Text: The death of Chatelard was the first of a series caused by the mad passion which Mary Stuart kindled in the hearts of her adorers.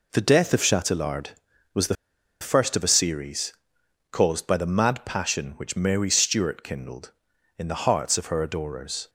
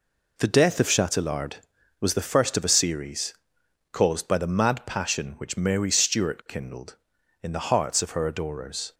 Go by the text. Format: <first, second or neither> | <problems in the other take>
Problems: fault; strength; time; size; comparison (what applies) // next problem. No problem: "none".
second | pauses between "the" and "first"; noticeable; at 1.9 s; 0.47 s long // pauses between "series" and "caused"; noticeable; at 3.5 s; 0.58 s long; noticeable in the second